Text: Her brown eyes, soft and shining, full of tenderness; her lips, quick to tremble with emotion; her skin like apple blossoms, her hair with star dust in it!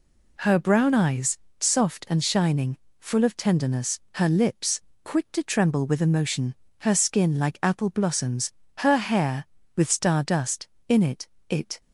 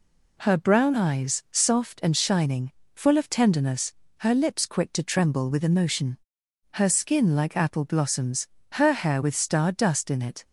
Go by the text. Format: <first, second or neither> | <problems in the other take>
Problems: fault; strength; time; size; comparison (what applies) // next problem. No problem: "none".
second | says "it" twice; at 11.4 s